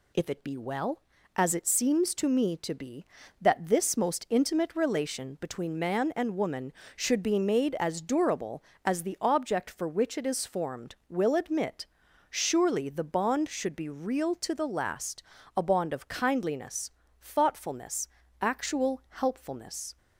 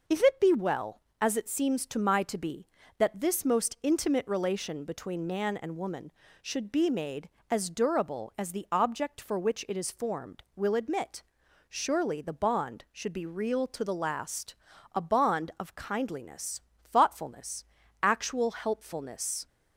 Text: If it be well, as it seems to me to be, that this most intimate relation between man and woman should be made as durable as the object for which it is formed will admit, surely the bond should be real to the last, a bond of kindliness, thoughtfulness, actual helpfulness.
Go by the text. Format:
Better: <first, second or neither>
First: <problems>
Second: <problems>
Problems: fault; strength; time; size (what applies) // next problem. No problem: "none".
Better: first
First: none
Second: says "my" for "me"; at 1.9 s